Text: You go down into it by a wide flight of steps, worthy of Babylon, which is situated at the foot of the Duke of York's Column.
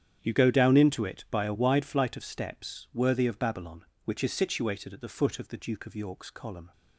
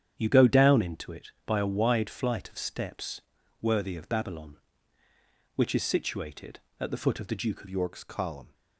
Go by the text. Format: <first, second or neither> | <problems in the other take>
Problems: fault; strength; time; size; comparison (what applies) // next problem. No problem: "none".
first | starts louder than the rest; strong; until 1.1 s; 9 dB; strong in the first // changes voice at "York's"; from 7.6 s on; 0.9 s long